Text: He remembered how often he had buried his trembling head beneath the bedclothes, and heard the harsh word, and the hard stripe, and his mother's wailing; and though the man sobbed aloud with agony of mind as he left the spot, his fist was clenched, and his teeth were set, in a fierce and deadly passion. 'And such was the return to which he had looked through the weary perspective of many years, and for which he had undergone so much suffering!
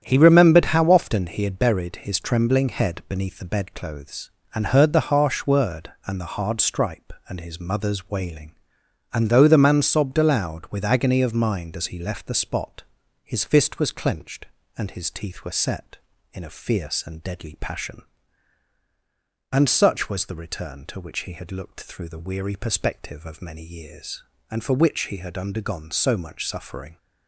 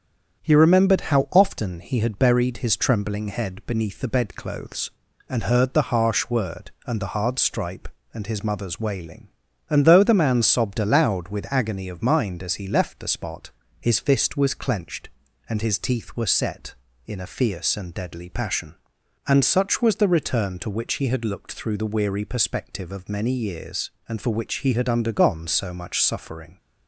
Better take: neither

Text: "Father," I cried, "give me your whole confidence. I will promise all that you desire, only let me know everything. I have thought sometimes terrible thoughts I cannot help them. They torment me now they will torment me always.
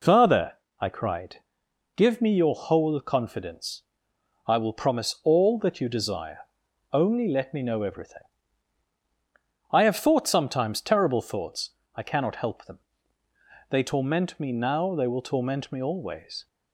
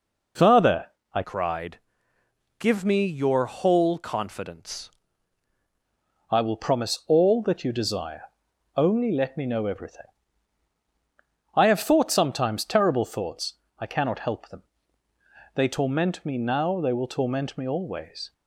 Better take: first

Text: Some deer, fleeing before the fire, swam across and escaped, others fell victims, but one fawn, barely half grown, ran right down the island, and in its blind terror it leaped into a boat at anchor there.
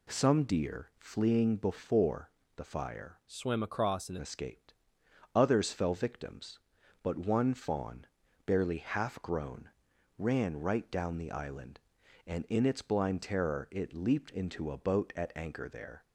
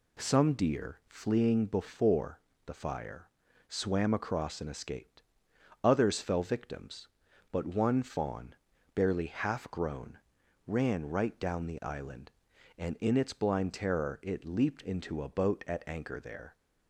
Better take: second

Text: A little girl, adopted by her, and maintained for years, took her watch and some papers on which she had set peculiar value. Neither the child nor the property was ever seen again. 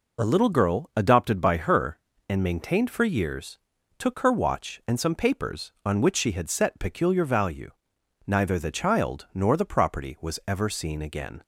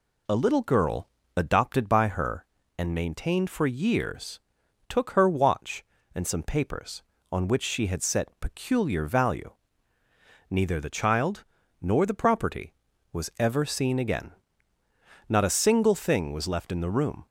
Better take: first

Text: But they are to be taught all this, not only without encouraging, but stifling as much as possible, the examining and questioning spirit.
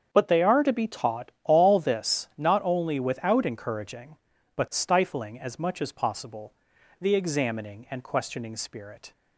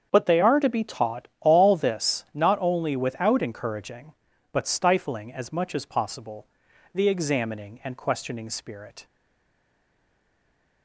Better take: first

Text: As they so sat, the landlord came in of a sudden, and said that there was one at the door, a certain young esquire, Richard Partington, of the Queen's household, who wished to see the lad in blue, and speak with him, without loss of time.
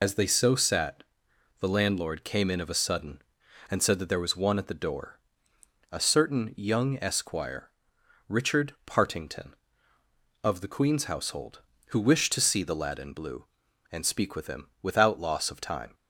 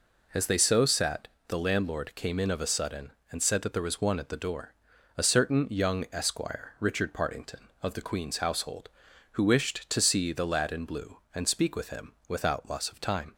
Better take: second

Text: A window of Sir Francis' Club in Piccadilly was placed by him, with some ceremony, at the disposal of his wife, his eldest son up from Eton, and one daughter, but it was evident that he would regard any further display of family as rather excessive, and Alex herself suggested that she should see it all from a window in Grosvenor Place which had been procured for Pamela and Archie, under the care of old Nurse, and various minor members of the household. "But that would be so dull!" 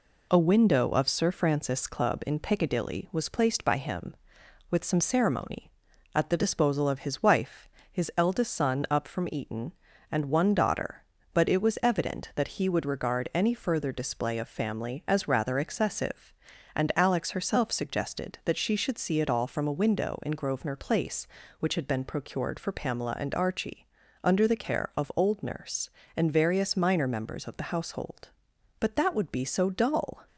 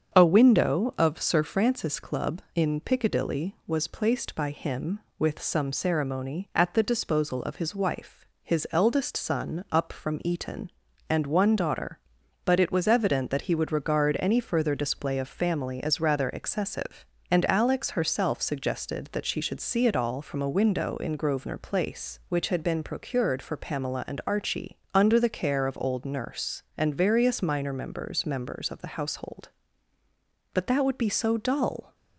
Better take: first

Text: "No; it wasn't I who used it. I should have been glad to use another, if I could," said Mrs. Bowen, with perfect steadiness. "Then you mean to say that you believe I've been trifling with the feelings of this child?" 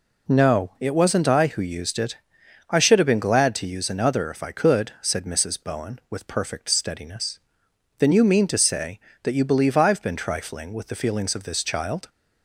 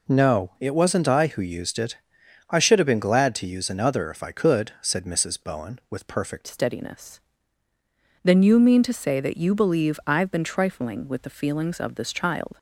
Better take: first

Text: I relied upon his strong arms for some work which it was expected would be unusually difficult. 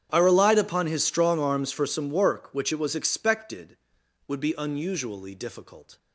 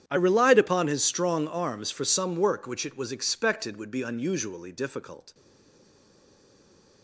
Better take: first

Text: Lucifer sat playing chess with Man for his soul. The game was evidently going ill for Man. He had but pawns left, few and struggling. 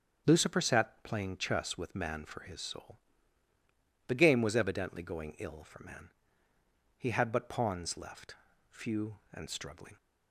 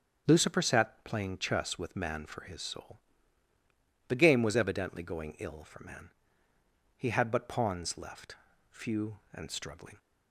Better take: neither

